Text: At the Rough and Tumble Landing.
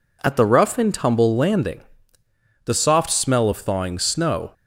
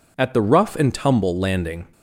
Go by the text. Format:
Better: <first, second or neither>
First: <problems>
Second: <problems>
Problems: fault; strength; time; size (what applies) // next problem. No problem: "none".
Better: second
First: goes on to say "The soft smell of thawing snow"; strong; from 2.6 s on; 1.8 s long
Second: none